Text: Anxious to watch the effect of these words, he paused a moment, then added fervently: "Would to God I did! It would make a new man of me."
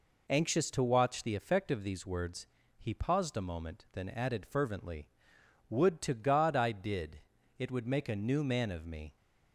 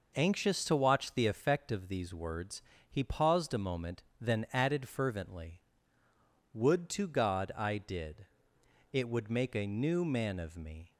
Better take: neither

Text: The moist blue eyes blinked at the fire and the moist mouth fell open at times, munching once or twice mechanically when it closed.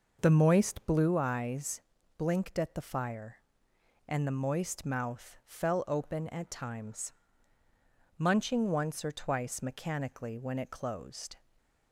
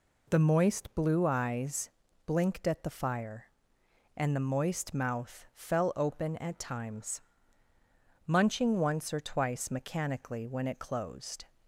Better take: second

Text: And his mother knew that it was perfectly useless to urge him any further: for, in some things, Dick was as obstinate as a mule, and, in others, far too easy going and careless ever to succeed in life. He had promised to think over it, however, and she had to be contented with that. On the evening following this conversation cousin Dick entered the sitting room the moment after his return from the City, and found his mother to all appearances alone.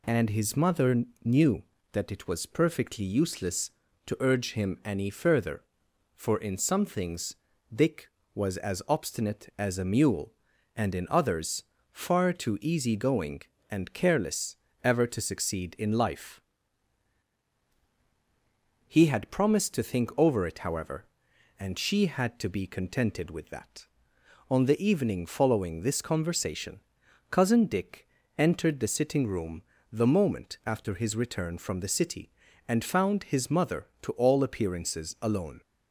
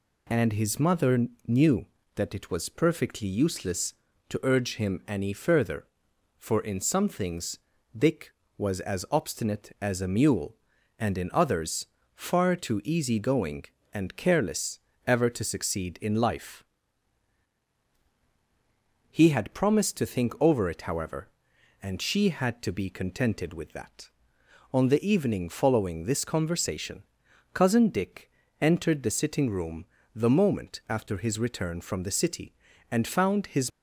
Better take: first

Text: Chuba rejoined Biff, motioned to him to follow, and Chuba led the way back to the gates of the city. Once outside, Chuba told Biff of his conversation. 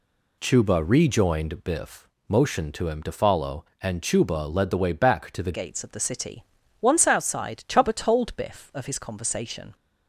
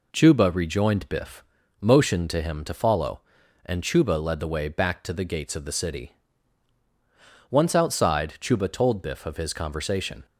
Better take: second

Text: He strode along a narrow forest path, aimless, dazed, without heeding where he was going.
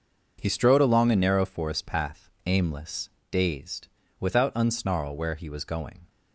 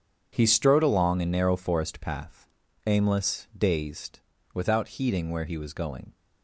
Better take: second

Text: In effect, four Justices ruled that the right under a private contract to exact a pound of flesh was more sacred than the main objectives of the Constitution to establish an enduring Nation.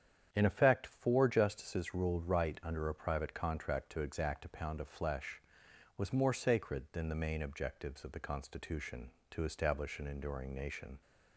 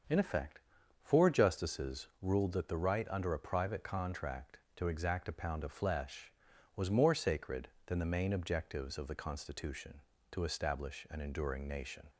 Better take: second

